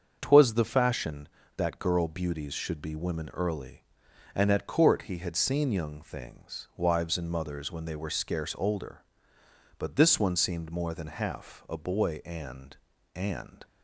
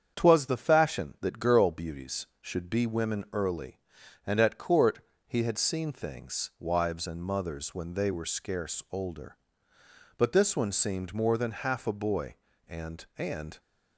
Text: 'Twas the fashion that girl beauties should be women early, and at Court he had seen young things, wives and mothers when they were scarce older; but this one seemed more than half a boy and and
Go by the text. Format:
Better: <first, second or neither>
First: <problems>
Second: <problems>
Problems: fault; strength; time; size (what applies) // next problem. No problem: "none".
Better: first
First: starts louder than the rest; until 1.2 s; 7 dB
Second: starts louder than the rest; strong; until 1.2 s; 7.5 dB // pauses between "Court" and "he"; slight; at 5.0 s; 0.26 s long // skips "young"; at 5.9 s